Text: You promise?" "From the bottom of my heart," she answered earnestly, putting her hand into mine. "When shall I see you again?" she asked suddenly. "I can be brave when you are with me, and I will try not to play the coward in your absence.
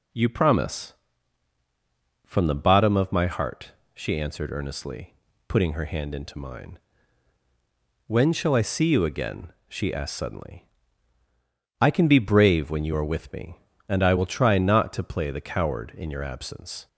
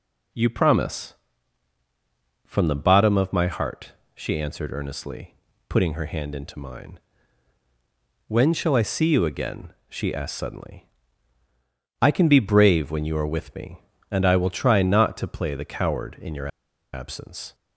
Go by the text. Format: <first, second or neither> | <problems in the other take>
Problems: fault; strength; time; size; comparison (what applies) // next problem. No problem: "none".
first | pauses between "your" and "absence"; at 16.4 s; 0.45 s long